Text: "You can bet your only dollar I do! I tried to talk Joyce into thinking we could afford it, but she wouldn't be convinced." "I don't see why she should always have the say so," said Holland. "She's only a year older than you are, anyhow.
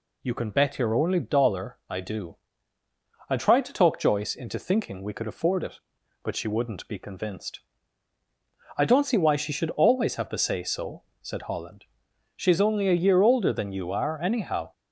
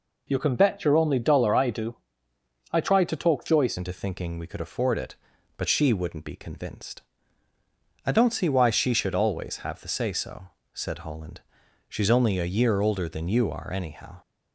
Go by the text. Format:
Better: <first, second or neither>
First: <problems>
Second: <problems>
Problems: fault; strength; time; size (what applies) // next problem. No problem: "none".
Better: first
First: none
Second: changes voice at "into"; from 3.7 s on; 10.5 s long